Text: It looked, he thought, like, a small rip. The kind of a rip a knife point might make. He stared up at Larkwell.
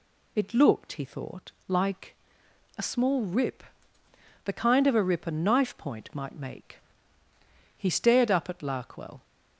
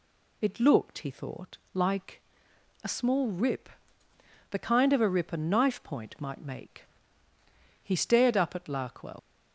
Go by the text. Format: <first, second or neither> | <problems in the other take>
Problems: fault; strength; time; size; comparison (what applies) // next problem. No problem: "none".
first | leaves "Larkwell" unfinished; at 9.1 s; 80 ms